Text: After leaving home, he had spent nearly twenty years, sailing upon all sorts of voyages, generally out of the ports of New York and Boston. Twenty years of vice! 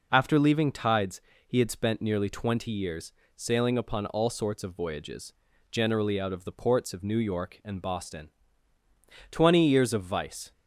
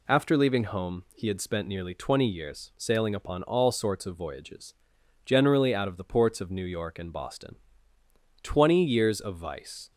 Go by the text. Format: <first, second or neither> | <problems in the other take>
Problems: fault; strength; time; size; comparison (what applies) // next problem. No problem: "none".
second | says "tides" for "home"; at 0.7 s